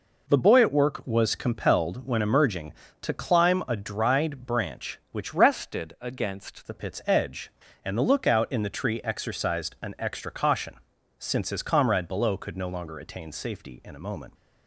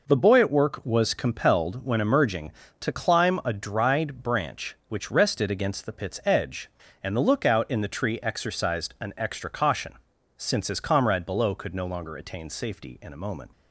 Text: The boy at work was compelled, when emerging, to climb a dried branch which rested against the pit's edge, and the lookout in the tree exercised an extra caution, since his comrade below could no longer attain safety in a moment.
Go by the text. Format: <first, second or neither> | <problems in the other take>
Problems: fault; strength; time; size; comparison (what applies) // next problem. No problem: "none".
second | changes voice from "rested" to "against"; from 5.3 to 6.6 s; 1.3 s long